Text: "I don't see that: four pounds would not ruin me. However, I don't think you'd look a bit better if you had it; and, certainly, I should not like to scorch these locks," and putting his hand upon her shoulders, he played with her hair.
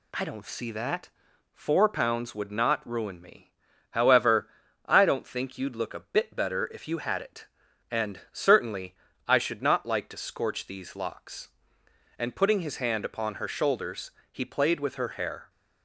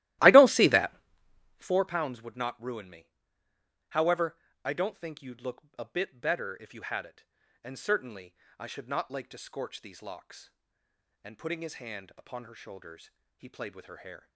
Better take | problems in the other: first | starts louder than the rest; strong; until 1.8 s; 16 dB // pauses between "look" and "a"; slight; at 5.6 s; 0.18 s long

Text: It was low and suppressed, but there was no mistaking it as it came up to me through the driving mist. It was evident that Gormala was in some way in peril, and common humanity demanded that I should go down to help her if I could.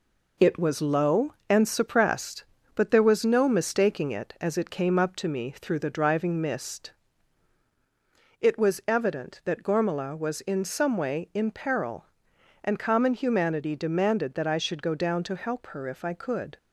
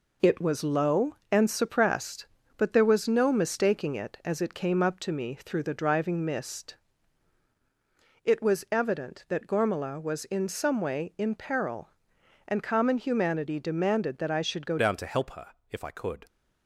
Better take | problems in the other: first | changes voice at "down"; from 14.7 s on; 1.5 s long // pauses between "her" and "if"; slight; at 15.4 s; 0.22 s long

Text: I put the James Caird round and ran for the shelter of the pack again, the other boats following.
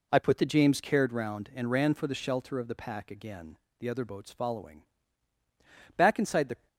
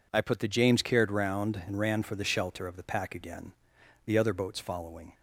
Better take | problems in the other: second | goes on to say "Back inside the"; noticeable; from 5.9 s on; 0.70 s long

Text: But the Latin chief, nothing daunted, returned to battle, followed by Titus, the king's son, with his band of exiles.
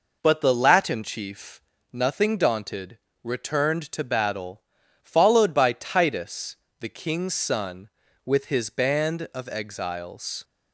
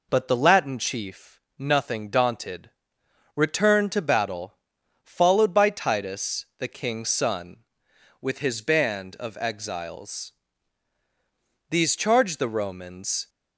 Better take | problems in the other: first | goes on to say "These charged the Romans"; from 11.6 s on; 1.6 s long

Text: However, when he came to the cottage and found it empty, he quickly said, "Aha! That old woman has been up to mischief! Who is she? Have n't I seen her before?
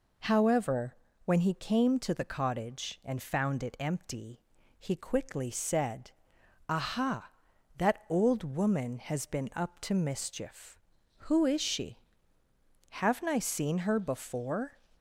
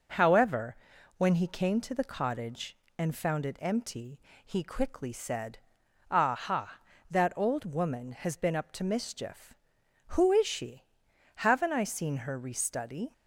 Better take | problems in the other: first | says "restudy" for "before"; at 12.3 s

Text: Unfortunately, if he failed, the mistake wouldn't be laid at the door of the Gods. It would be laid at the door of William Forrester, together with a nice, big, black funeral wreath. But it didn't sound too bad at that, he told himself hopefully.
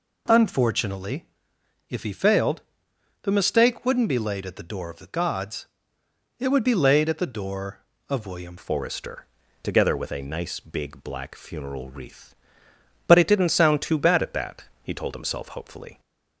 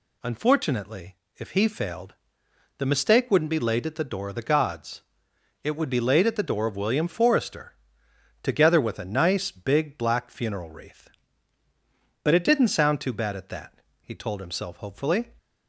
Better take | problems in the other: second | changes voice at "Forrester"; from 8.5 s on; 7.4 s long

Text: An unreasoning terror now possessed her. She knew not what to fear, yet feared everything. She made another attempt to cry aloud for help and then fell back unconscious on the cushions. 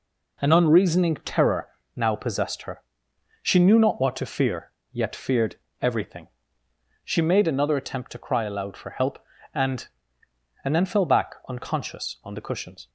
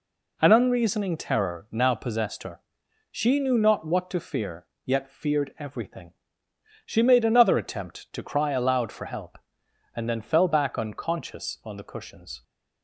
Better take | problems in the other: second | pauses between "terror" and "now"; slight; at 1.6 s; 0.30 s long // pauses between "feared" and "everything"; slight; at 5.5 s; 0.24 s long // says "and" twice; at 10.6 s

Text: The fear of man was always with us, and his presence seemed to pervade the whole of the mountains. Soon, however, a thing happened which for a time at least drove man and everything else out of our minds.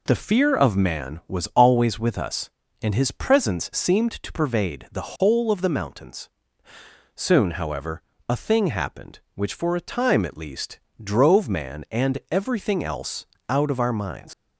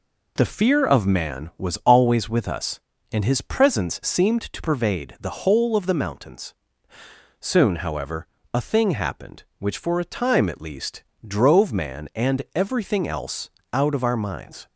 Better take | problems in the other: second | pauses between "least" and "drove"; slight; at 10.8 s; 0.20 s long; slight in the second // pauses between "else" and "out"; slight; at 13.2 s; 0.24 s long; slight in the second // leaves "minds" unfinished; at 14.3 s; 90 ms

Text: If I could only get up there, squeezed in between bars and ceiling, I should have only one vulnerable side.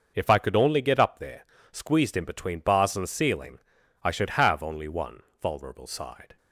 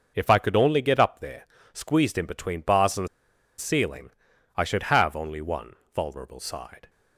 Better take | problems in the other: first | pauses between "and" and "ceiling"; noticeable; at 3.0 s; 0.51 s long // pauses between "one" and "vulnerable"; slight; at 5.7 s; 0.20 s long; slight in the first

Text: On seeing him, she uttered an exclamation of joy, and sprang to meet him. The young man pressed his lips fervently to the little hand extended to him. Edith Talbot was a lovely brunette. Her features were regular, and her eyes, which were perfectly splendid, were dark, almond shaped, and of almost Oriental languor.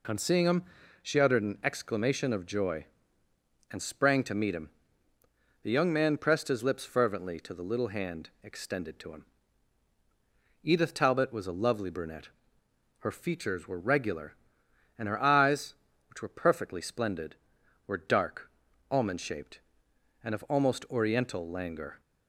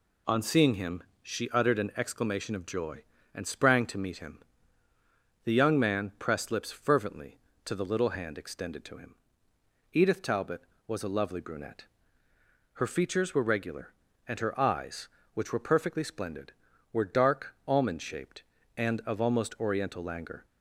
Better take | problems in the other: first | skips "his"; at 6.5 s

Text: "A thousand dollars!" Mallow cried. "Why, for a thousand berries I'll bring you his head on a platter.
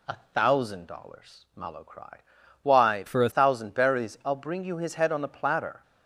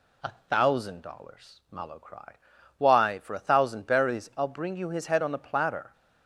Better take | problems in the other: second | pauses between "A" and "thousand"; slight; at 0.1 s; 0.18 s long; slight in the second // changes voice from "for" to "a"; from 3.0 to 3.3 s; 0.3 s long

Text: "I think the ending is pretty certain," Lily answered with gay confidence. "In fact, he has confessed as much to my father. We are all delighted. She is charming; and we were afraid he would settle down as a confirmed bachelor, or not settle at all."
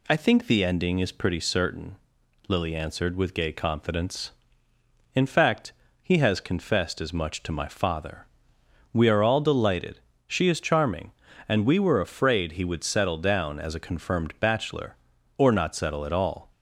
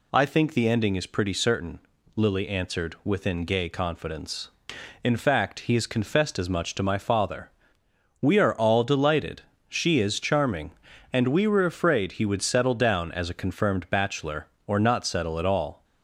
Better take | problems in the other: first | says "within" for "with"; at 3.0 s

